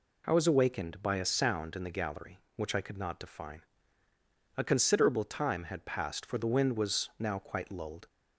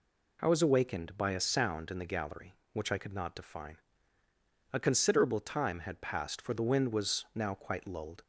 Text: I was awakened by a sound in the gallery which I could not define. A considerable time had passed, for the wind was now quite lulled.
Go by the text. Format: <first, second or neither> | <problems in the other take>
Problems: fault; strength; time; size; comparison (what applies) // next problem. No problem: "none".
neither | none